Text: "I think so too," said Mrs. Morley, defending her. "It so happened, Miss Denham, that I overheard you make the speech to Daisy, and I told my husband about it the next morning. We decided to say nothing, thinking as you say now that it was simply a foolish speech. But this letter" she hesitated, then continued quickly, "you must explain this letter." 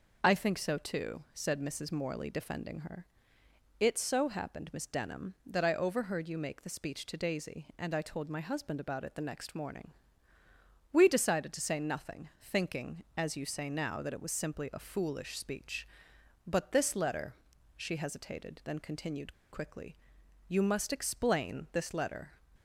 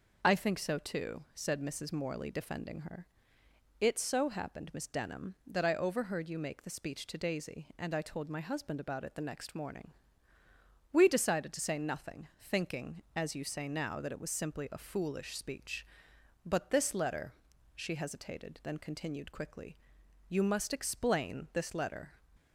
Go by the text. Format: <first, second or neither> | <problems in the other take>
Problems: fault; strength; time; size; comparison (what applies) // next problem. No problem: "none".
second | pauses between "letter" and "she"; at 17.3 s; 0.42 s long; also in the second // pauses between "continued" and "quickly"; slight; at 19.3 s; 0.20 s long